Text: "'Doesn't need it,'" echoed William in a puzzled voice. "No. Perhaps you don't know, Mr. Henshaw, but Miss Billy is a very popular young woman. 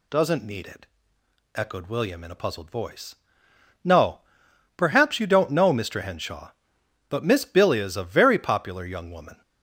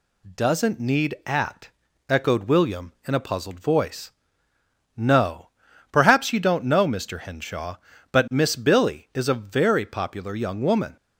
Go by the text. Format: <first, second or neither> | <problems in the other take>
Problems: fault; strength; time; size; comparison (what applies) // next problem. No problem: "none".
first | says "at" for "it"; at 1.2 s